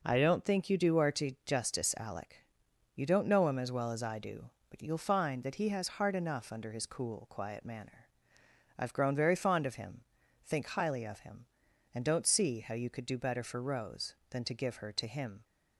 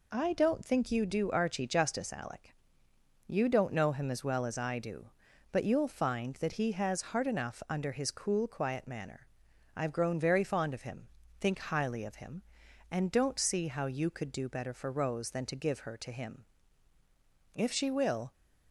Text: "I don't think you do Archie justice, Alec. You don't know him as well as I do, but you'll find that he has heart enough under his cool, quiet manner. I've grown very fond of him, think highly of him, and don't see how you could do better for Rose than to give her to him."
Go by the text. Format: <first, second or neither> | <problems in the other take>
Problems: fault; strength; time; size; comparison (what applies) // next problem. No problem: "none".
first | goes on to say "If she will"; noticeable; from 17.5 s on; 0.78 s long